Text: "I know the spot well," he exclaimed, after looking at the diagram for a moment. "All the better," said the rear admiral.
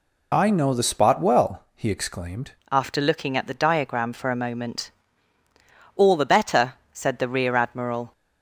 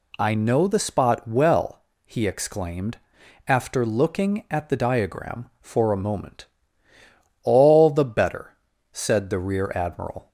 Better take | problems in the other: second | changes voice at "after"; from 2.6 s on; 5.5 s long

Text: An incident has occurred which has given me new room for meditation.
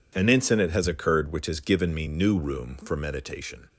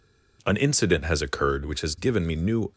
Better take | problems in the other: first | stops before "room for meditation"; at 2.7 s

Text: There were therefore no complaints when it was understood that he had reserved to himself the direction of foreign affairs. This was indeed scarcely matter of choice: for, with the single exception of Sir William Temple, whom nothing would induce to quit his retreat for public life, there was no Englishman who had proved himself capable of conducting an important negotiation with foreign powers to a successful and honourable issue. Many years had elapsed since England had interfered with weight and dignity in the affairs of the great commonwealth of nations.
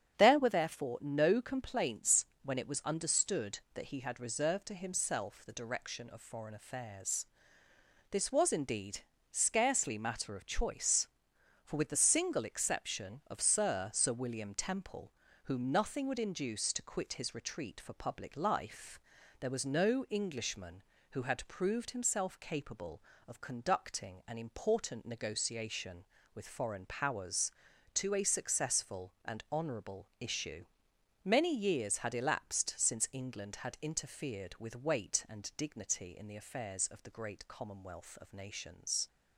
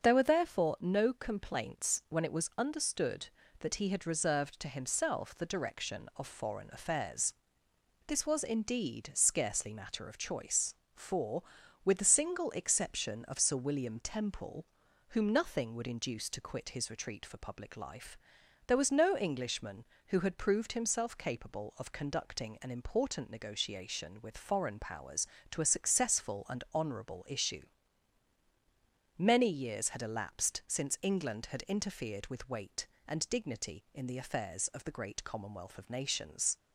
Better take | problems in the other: second | starts louder than the rest; strong; until 1.1 s; 8 dB; also in the second // pauses between "complaints" and "when"; slight; at 2.2 s; 0.18 s long // pauses between "indeed" and "scarcely"; slight; at 9.0 s; 0.32 s long // says "Sir" twice; at 13.9 s

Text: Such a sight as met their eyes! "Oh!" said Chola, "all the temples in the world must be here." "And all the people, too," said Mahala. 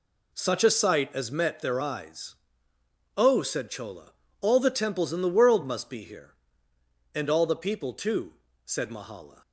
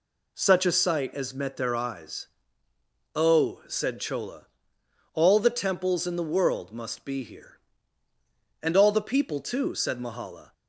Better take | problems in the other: neither | none

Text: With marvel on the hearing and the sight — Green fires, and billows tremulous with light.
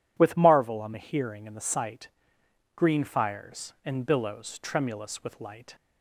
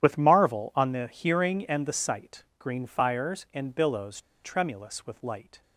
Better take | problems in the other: first | starts louder than the rest; strong; until 1.0 s; 10.5 dB // pauses between "billows" and "tremulous"; slight; at 4.2 s; 0.23 s long

